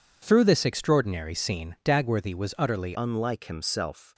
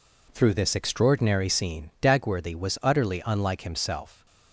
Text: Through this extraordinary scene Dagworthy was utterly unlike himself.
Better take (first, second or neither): second